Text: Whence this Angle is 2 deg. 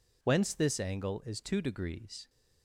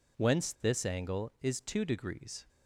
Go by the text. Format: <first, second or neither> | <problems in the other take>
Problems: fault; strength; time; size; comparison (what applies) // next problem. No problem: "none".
neither | none